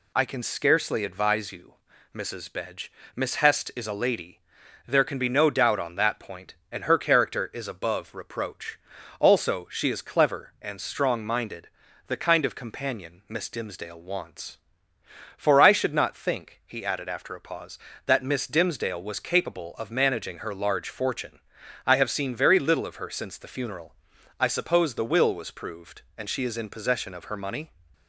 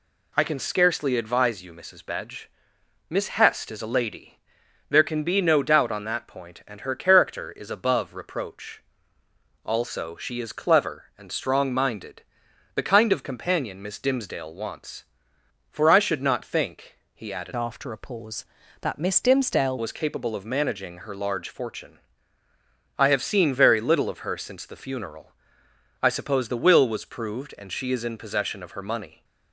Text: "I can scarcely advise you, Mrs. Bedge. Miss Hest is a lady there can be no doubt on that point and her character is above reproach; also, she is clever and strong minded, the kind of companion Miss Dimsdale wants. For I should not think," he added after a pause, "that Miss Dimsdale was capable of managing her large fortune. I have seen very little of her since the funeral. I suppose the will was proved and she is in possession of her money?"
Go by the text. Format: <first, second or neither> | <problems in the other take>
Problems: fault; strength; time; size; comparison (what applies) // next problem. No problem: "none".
first | pauses between "lady" and "there"; noticeable; at 4.3 s; 0.52 s long; noticeable in the first // changes voice from "after" to "Dimsdale"; from 17.5 to 19.7 s; 2.2 s long